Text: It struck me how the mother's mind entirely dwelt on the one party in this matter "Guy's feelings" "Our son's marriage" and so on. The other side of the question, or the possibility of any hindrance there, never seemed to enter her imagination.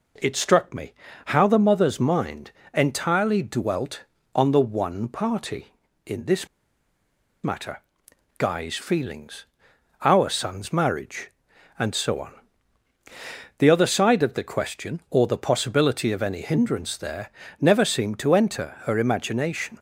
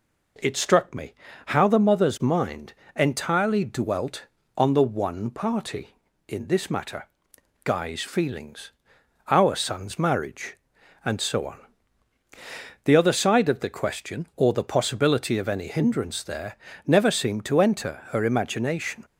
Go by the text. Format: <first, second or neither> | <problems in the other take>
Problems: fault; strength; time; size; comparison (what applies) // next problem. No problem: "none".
second | pauses between "me" and "how"; slight; at 0.9 s; 0.34 s long; slight in the second // pauses between "mind" and "entirely"; slight; at 2.5 s; 0.22 s long; slight in the second // pauses between "this" and "matter"; noticeable; at 6.4 s; 0.97 s long // pauses between "matter" and "Guy's"; noticeable; at 7.8 s; 0.58 s long; noticeable in the second // pauses between "feelings" and "Our"; noticeable; at 9.4 s; 0.58 s long; noticeable in the second